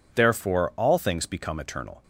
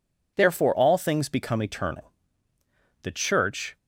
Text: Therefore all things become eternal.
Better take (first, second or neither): first